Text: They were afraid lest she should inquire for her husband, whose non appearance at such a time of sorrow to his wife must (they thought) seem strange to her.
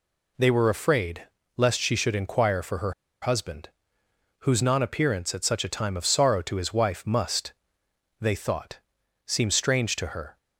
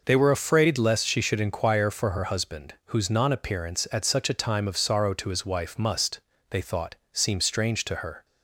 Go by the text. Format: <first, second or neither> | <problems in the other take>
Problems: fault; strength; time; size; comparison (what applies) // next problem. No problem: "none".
second | pauses between "afraid" and "lest"; slight; at 1.2 s; 0.30 s long // pauses between "her" and "husband"; slight; at 2.9 s; 0.29 s long